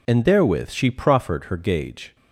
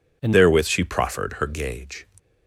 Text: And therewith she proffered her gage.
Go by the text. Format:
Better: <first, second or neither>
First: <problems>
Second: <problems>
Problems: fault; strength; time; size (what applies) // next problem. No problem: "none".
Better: first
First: none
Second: changes voice at "therewith"; from 0.3 s on; 1.7 s long